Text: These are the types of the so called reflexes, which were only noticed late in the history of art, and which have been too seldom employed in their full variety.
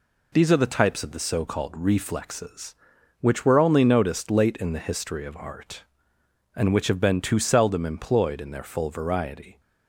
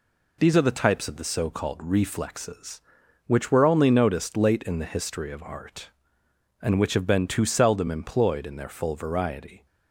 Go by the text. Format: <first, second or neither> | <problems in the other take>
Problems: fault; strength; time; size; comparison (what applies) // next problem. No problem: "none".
neither | none